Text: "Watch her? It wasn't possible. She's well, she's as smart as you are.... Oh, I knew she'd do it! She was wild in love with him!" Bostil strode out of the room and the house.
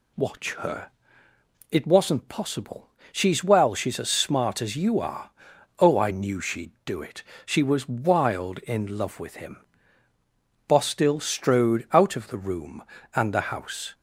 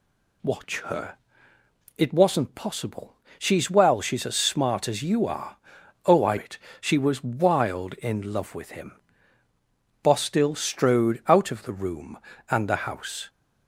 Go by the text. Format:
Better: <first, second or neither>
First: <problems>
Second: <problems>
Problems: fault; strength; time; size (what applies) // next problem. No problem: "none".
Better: first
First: none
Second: skips "knew she'd do"; at 6.3 s